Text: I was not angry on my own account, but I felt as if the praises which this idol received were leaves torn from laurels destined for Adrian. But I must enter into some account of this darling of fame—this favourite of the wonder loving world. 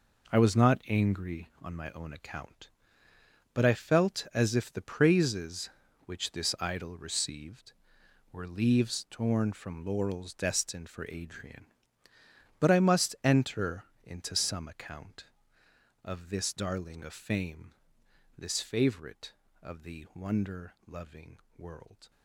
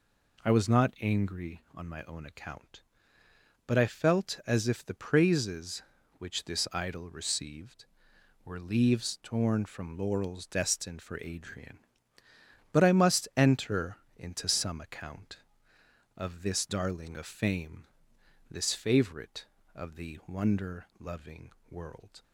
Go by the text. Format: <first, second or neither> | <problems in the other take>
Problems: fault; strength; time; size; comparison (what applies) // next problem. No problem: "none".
second | gets quieter; strong; throughout; 10 dB // pauses between "enter" and "into"; slight; at 13.8 s; 0.18 s long; slight in the second // pauses between "loving" and "world"; slight; at 21.3 s; 0.18 s long; slight in the second